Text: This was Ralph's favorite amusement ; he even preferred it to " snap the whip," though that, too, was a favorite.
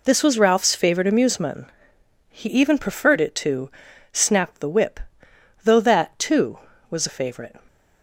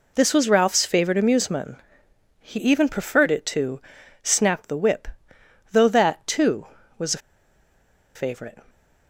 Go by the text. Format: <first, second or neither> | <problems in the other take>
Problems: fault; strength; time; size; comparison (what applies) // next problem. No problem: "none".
first | pauses between "a" and "favorite"; noticeable; at 7.1 s; 0.97 s long